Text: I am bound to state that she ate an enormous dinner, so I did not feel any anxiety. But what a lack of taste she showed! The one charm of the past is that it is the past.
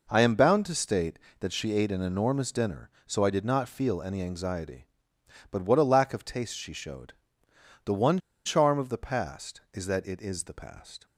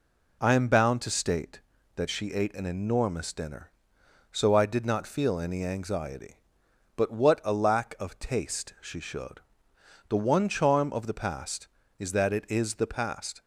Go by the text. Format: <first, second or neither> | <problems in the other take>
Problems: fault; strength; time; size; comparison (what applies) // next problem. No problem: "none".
second | pauses between "one" and "charm"; slight; at 8.1 s; 0.27 s long